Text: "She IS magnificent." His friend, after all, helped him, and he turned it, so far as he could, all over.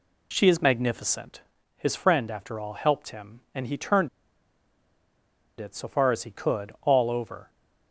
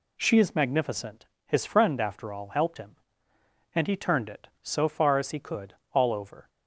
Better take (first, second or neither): second